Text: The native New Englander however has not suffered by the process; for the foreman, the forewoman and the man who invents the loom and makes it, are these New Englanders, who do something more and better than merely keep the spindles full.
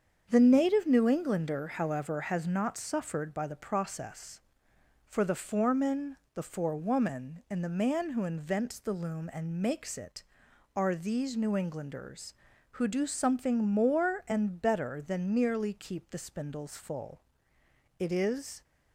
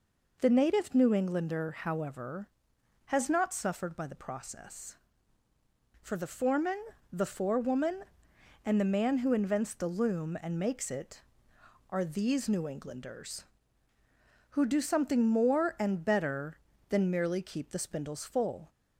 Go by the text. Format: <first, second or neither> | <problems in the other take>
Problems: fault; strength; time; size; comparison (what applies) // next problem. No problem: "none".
second | starts louder than the rest; strong; until 1.3 s; 7 dB // goes on to say "It is"; noticeable; from 17.9 s on; 0.64 s long